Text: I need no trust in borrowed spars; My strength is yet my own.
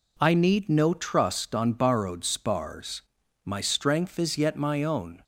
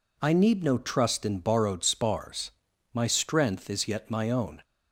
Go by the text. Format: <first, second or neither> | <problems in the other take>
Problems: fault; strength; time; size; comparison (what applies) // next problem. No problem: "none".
second | says "on" for "in"; at 1.5 s